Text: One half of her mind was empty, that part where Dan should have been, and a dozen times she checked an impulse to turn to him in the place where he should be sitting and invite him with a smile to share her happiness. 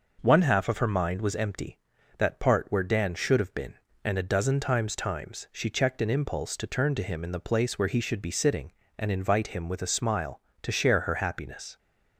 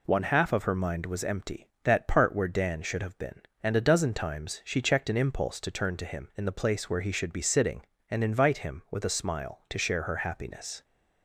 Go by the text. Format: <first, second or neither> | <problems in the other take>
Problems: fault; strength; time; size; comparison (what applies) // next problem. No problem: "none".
second | says "times" twice; at 4.9 s